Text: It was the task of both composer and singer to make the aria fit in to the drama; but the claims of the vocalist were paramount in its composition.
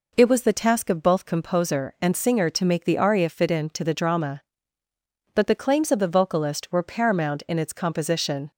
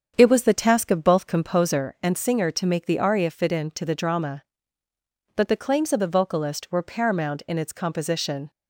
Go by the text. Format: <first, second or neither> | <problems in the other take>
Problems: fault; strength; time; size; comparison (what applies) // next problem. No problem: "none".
first | starts louder than the rest; strong; until 2.0 s; 7.5 dB